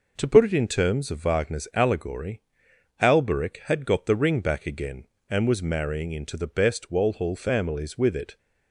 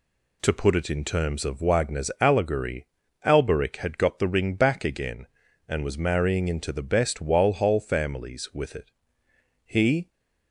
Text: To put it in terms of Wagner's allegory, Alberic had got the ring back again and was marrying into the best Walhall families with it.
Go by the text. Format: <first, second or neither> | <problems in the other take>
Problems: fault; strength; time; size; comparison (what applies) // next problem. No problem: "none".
first | goes on to say "He"; slight; from 9.6 s on; 0.44 s long